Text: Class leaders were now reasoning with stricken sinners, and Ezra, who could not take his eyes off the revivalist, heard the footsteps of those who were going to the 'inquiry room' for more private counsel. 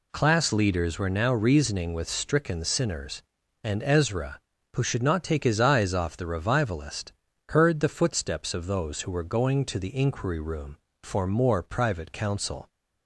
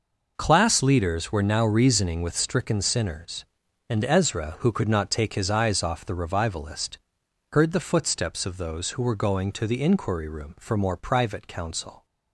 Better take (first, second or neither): second